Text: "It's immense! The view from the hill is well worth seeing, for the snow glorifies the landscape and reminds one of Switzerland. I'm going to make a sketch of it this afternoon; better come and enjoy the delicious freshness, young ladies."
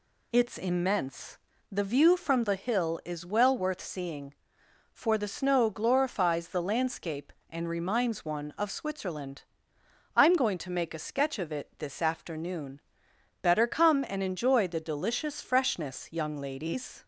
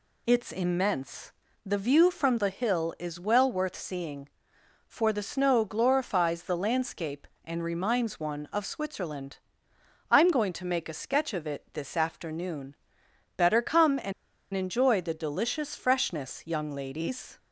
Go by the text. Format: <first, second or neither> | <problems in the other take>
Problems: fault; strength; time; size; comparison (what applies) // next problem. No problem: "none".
first | pauses between "and" and "enjoy"; at 14.1 s; 0.41 s long